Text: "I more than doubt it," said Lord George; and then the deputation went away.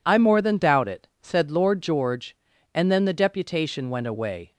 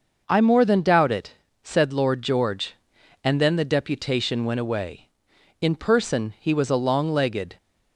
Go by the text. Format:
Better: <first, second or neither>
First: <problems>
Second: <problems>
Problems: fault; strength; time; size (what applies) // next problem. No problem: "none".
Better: first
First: none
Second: goes on to say "In person he was a long legged"; strong; from 5.6 s on; 1.9 s long